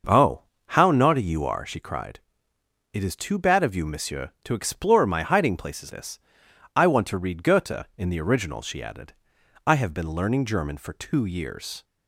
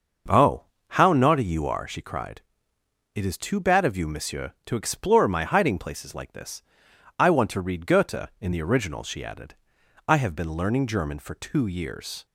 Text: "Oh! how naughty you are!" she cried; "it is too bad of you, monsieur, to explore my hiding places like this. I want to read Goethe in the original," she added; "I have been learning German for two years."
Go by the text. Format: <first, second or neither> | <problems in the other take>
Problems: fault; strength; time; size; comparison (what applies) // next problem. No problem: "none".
second | starts louder than the rest; noticeable; until 1.3 s; 6 dB; also in the second // skips "like"; at 5.9 s